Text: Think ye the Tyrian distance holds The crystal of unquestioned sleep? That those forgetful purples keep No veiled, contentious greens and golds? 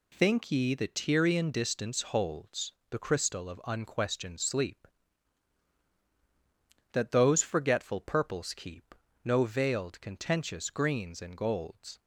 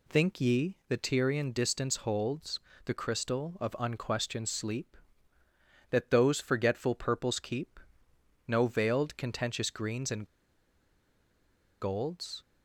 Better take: first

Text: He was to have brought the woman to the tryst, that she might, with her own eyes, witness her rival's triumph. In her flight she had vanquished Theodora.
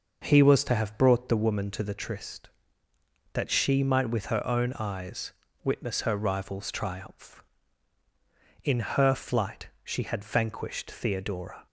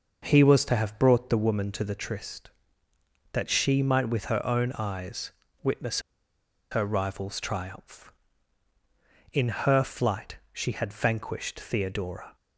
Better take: first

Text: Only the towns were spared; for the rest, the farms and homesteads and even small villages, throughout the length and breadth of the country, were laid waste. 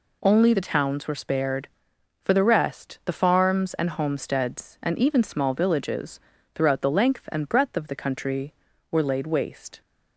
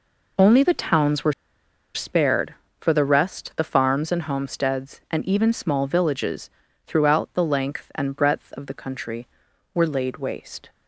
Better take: first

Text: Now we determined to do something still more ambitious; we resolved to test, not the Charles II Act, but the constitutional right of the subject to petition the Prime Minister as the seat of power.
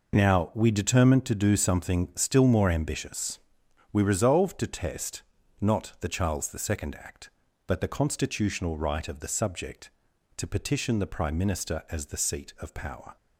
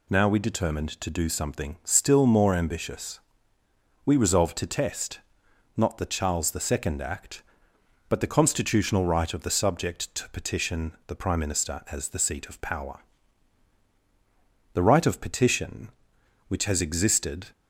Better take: first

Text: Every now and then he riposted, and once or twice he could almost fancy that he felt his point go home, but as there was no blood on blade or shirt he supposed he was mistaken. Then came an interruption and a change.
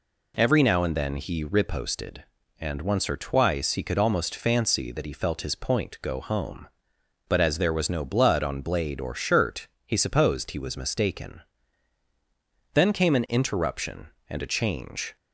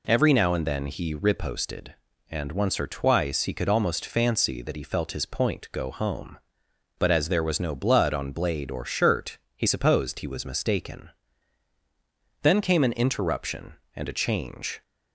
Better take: neither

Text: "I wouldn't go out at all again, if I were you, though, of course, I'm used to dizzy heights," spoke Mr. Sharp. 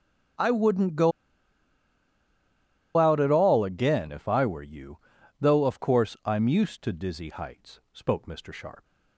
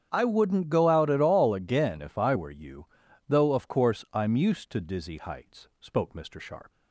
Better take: second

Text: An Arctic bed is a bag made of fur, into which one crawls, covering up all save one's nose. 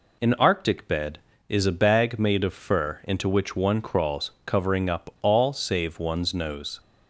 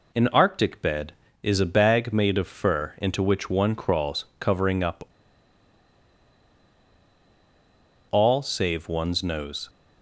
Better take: first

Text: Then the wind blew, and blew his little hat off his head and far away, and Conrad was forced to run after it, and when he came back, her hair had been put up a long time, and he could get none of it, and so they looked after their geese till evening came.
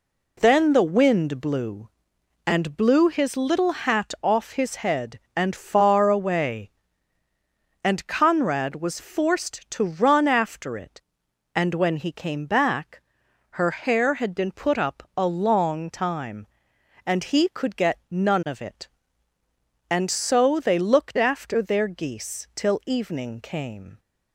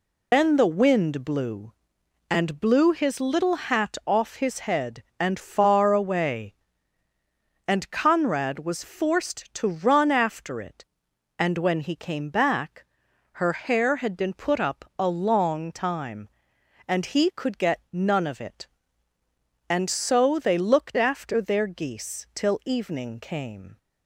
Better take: first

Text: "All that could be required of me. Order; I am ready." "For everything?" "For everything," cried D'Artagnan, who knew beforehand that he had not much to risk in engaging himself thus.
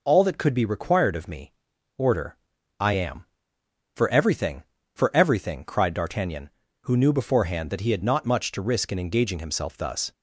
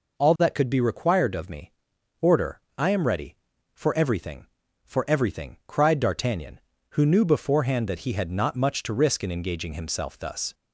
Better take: second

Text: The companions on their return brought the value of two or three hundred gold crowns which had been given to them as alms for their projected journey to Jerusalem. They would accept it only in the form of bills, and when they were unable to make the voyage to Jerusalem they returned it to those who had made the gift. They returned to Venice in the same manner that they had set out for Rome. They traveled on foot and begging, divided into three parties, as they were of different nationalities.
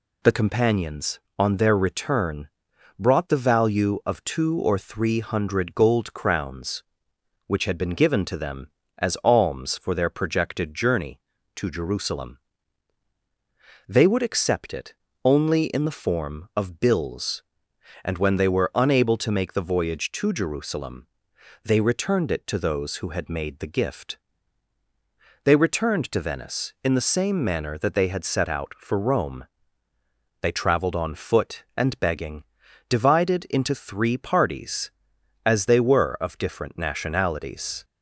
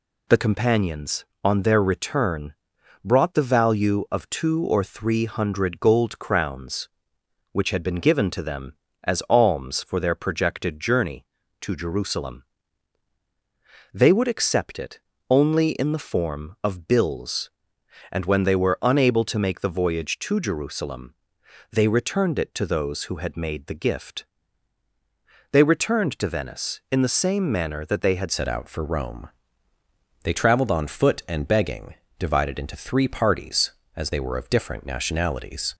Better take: first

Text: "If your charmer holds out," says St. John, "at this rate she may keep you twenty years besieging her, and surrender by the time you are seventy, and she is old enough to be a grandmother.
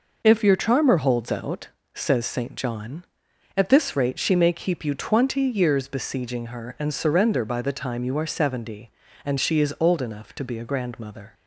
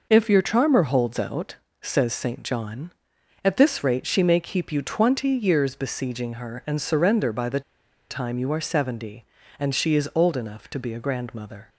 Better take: first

